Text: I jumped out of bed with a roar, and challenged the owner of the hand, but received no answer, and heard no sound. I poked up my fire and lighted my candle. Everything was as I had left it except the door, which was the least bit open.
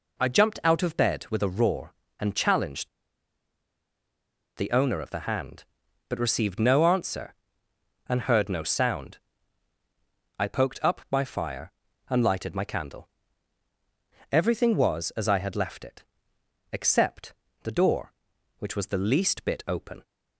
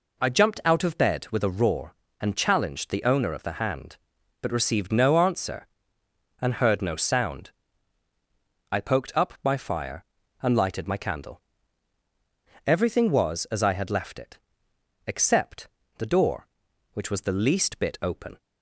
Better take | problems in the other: second | pauses between "challenged" and "the"; strong; at 2.8 s; 1.6 s long // pauses between "it" and "except"; noticeable; at 16.0 s; 0.70 s long; noticeable in the second // pauses between "except" and "the"; slight; at 17.3 s; 0.28 s long; slight in the second

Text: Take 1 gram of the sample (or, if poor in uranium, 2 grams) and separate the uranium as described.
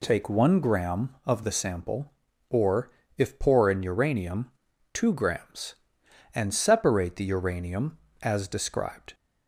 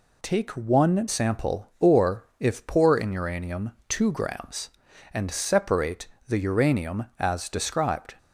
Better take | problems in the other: first | skips "gram of the"; at 1.0 s // pauses between "separate" and "the"; slight; at 6.0 s; 0.20 s long

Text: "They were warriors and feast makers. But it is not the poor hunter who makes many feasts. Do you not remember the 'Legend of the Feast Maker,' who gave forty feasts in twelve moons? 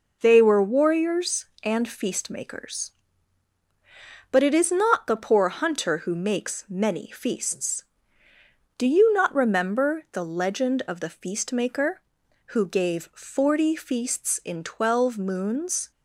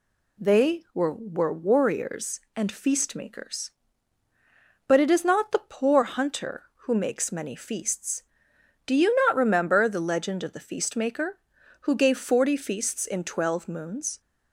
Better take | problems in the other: first | says "were" twice; at 1.1 s

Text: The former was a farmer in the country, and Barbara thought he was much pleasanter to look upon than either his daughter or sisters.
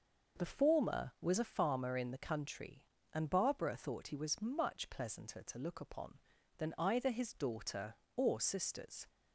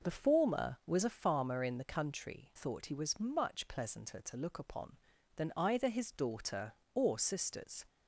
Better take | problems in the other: first | skips "and Barbara"; at 2.5 s

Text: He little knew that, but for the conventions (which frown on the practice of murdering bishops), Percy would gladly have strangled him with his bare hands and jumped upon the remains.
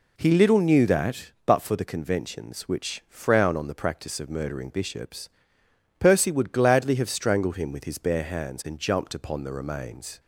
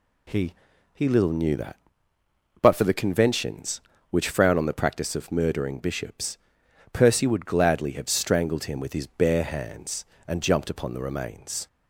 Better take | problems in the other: first | says "He" twice; at 0.9 s

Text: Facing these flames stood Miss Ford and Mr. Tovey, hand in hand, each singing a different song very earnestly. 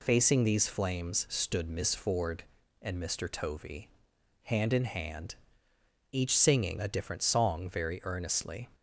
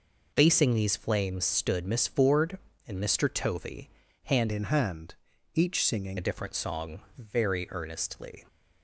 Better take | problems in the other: first | changes voice from "in" to "singing"; from 4.5 to 6.1 s; 1.6 s long // pauses between "song" and "very"; slight; at 7.0 s; 0.16 s long

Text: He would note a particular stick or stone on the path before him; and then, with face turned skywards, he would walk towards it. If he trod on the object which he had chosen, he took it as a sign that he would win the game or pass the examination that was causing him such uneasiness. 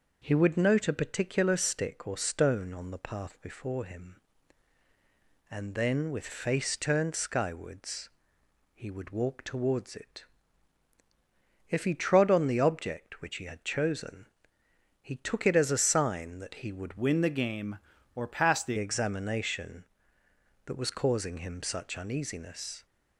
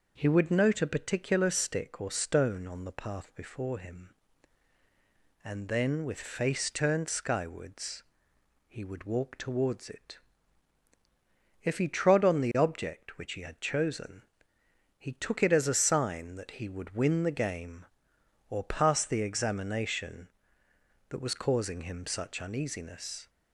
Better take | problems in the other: second | changes voice from "win" to "the"; from 16.9 to 18.7 s; 1.8 s long

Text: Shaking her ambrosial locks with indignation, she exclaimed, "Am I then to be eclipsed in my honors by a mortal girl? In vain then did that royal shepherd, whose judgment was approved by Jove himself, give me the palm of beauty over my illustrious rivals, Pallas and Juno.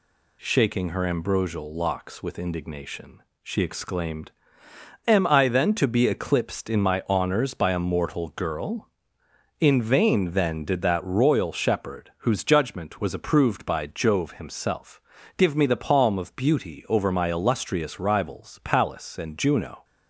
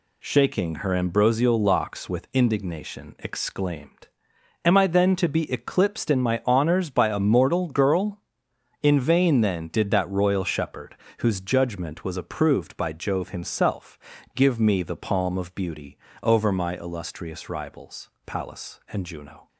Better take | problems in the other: first | skips "she"; at 3.1 s // pauses between "beauty" and "over"; slight; at 15.9 s; 0.24 s long

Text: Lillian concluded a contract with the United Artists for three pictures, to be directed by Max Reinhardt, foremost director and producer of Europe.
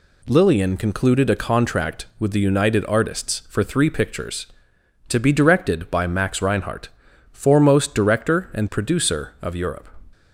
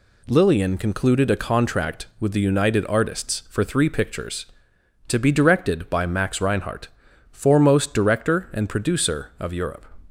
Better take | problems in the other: neither | none

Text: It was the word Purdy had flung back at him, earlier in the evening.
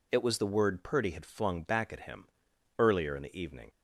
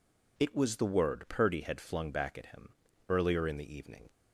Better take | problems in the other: neither | none

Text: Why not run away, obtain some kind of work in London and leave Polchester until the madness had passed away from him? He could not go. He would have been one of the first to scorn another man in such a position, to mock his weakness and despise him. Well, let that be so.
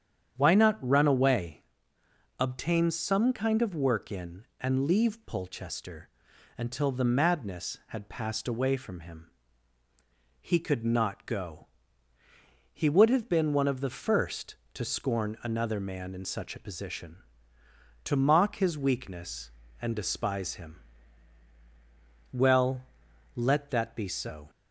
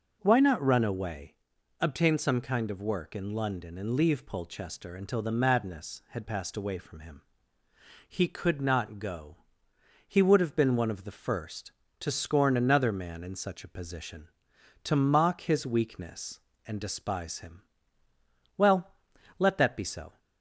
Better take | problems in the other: second | starts louder than the rest; strong; until 1.4 s; 8.5 dB // skips "London"; at 4.5 s // pauses between "Polchester" and "until"; noticeable; at 6.0 s; 0.46 s long

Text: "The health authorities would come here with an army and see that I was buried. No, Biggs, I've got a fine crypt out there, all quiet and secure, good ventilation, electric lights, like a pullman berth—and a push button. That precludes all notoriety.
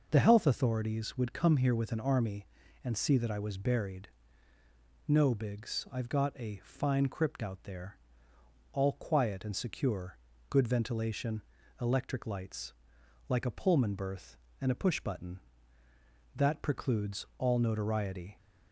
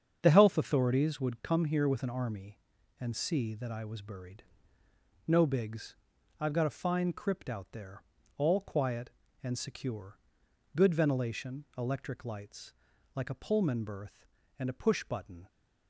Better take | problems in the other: first | starts louder than the rest; strong; until 1.2 s; 7.5 dB // stops before "That precludes all notoriety"; at 15.4 s

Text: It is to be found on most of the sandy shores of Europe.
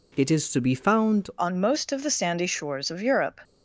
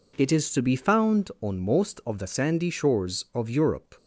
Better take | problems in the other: second | changes voice at "on"; from 1.3 s on; 2.1 s long

